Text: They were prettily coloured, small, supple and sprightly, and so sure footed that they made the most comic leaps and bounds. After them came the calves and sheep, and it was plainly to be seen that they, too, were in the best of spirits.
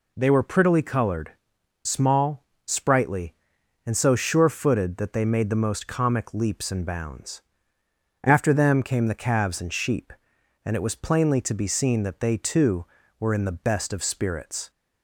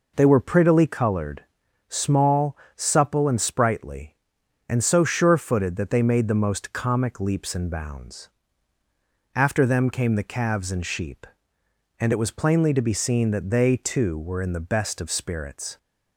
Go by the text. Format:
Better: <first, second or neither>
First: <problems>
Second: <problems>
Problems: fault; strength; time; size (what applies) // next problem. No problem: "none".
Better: second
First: skips "supple and"; at 2.5 s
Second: none